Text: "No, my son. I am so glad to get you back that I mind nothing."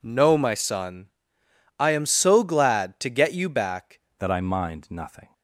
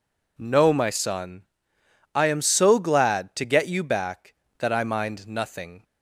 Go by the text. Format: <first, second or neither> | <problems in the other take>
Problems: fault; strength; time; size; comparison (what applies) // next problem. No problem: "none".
second | changes voice at "that"; from 4.1 s on; 1.2 s long